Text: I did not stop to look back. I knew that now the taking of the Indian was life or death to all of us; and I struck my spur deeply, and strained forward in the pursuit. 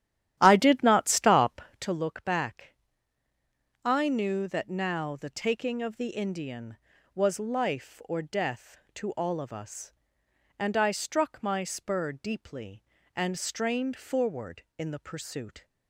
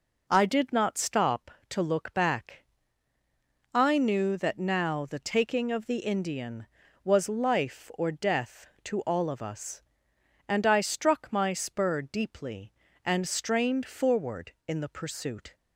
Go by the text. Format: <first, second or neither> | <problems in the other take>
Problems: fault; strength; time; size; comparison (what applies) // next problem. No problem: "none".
second | starts louder than the rest; strong; until 1.9 s; 12 dB